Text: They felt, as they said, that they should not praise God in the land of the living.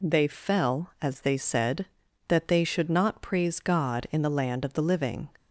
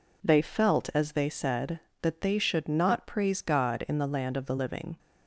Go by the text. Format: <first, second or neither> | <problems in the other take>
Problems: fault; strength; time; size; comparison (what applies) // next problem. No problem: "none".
second | says "fell" for "felt"; at 0.2 s